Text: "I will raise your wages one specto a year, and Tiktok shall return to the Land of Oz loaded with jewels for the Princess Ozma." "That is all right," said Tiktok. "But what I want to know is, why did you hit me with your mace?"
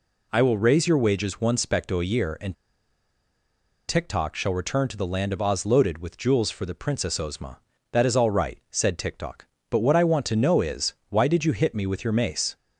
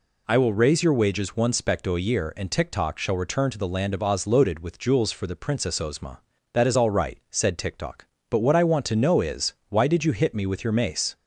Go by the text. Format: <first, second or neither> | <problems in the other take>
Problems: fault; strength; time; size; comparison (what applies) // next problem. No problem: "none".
second | pauses between "and" and "Tiktok"; strong; at 2.5 s; 1.3 s long